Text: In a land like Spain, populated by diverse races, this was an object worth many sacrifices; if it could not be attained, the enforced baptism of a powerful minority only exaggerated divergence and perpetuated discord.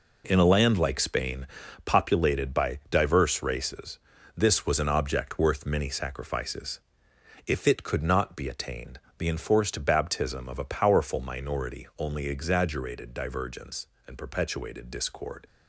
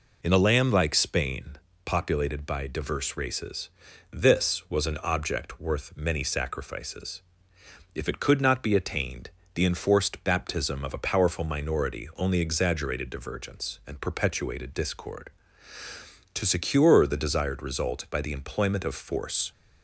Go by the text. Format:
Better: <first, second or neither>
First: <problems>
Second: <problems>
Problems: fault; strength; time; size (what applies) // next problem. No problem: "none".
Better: first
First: none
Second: goes on to say "To secure the desired result by the employment of force"; strong; from 16.3 s on; 3.1 s long